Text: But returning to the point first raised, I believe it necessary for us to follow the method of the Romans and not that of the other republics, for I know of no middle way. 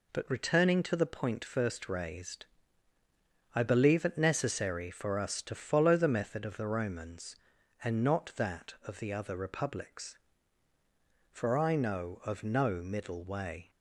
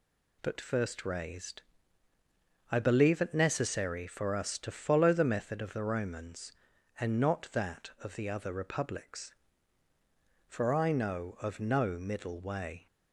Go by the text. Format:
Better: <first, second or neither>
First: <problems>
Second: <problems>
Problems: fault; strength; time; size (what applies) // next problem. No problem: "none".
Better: first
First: none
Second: skips "returning to the point"; at 0.5 s